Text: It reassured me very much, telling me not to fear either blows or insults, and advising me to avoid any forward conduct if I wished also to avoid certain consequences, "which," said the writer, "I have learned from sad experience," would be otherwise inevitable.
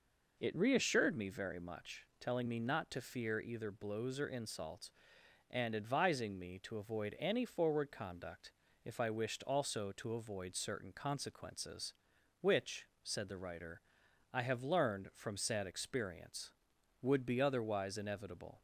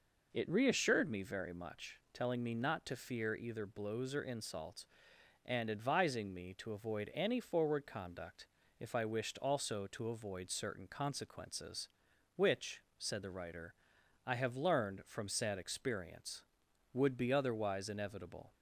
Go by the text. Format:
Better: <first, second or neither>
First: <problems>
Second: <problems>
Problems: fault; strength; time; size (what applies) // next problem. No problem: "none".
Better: neither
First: pauses between "conduct" and "if"; slight; at 8.5 s; 0.32 s long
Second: pauses between "conduct" and "if"; slight; at 8.4 s; 0.32 s long